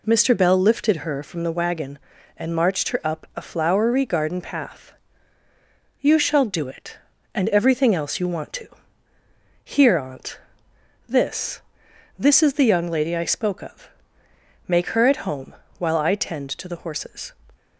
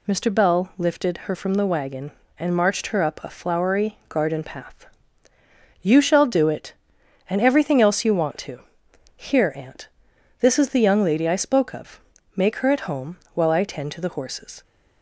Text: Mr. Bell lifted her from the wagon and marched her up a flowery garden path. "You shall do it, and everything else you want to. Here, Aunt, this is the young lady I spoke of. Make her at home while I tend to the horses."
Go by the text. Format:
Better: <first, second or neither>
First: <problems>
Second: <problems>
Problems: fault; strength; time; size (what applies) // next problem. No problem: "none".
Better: second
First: says "this" twice; at 12.1 s // pauses between "home" and "while"; slight; at 15.5 s; 0.24 s long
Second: pauses between "home" and "while"; slight; at 13.1 s; 0.18 s long